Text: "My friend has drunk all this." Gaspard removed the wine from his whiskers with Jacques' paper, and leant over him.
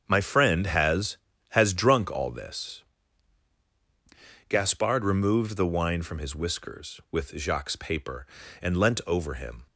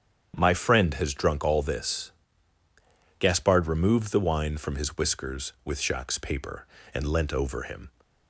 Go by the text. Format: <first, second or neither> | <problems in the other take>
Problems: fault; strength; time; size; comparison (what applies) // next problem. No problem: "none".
second | starts louder than the rest; strong; until 1.0 s; 7.5 dB; strong in the second // says "has" twice; at 1.4 s